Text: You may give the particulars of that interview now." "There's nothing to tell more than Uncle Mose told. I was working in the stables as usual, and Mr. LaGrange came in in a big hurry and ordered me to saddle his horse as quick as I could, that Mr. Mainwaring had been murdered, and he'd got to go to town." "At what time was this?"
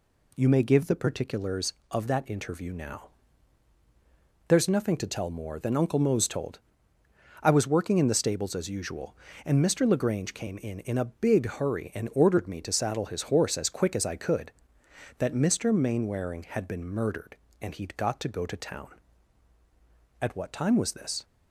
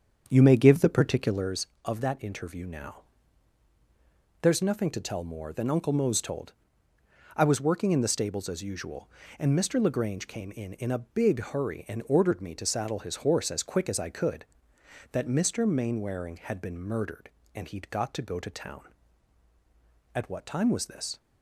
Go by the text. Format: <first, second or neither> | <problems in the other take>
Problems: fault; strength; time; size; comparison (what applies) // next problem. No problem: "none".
first | starts louder than the rest; strong; until 1.5 s; 7.5 dB